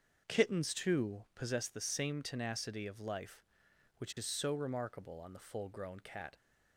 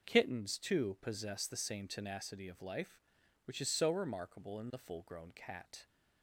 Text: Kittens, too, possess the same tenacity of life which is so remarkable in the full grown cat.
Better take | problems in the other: second | starts louder than the rest; until 1.2 s; 6.5 dB // says "on" for "in"; at 5.1 s

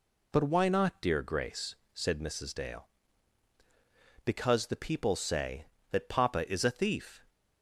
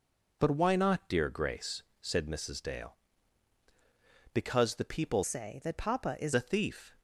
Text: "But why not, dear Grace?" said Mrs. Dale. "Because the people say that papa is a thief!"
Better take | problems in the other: first | changes voice from "say" to "is"; from 5.2 to 6.3 s; 1.1 s long

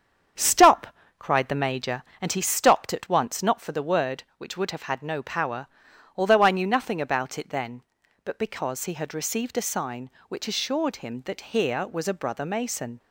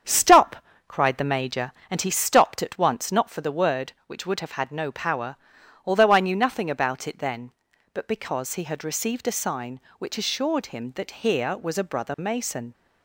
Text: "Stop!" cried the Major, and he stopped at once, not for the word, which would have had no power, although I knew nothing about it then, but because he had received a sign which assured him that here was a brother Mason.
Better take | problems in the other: neither | starts louder than the rest; strong; the same in both

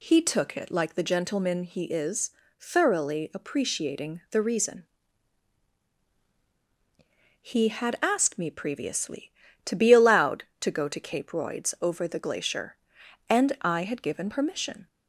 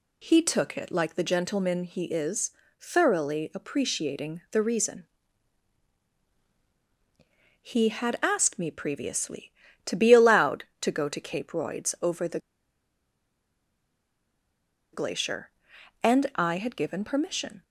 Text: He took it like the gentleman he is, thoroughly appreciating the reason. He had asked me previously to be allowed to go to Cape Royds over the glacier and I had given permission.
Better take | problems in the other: first | pauses between "the" and "glacier"; strong; at 12.3 s; 2.5 s long

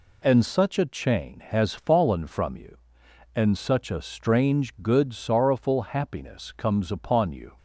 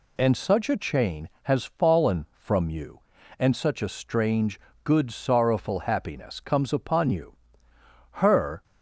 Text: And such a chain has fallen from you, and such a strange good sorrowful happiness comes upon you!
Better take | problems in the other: first | pauses between "strange" and "good"; slight; at 4.5 s; 0.24 s long // goes on to say "Her"; from 8.1 s on; 0.50 s long

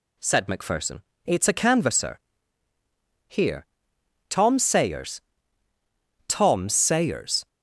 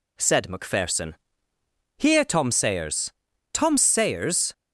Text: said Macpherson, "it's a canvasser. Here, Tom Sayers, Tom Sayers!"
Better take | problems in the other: first | skips "it's a canvasser"; at 1.5 s

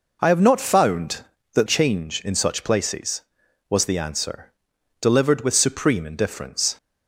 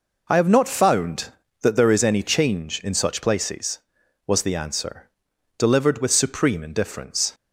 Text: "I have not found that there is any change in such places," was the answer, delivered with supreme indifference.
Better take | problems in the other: second | skips "there is any"; at 1.6 s

